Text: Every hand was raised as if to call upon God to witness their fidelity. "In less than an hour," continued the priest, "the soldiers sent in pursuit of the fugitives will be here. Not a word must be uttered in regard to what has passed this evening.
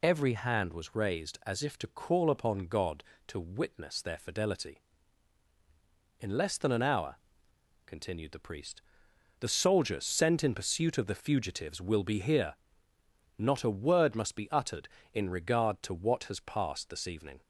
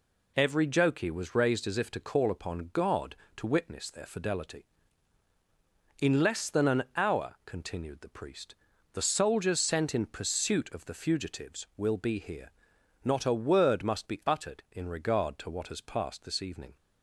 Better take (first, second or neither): first